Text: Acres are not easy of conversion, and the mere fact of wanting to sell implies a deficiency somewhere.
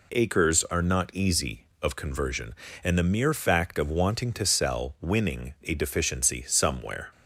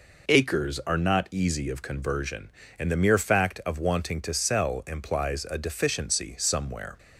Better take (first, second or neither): second